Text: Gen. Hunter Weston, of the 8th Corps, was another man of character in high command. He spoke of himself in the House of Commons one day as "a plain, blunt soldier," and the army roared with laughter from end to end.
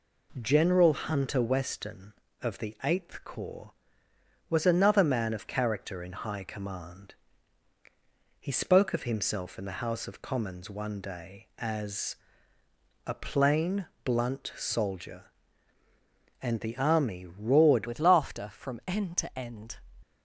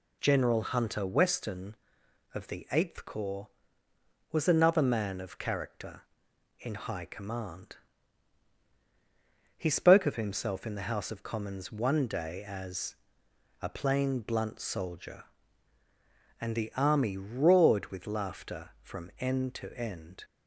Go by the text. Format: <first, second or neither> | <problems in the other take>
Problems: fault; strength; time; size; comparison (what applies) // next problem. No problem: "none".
second | pauses between "as" and "a"; noticeable; at 12.1 s; 0.90 s long; noticeable in the second // changes voice at "with"; from 17.8 s on; 1.9 s long